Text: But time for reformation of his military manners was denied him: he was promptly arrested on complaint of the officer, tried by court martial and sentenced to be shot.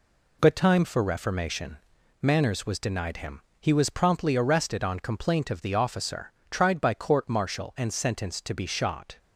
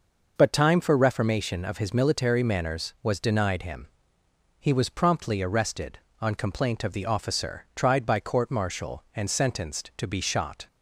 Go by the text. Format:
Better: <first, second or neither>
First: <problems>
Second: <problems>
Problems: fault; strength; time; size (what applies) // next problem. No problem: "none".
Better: second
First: skips "of his military"; at 1.9 s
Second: none